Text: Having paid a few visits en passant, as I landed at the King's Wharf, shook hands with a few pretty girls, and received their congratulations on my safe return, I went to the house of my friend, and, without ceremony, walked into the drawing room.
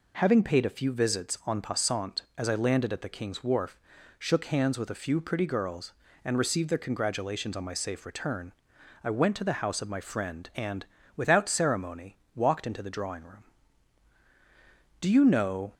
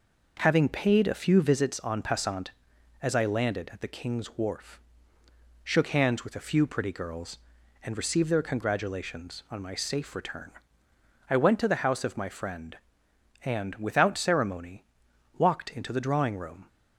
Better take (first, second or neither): second